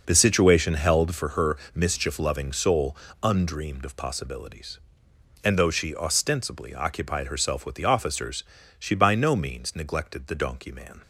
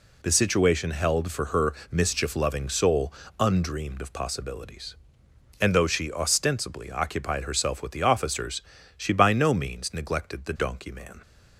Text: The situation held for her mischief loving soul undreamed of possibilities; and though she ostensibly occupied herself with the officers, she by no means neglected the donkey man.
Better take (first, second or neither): second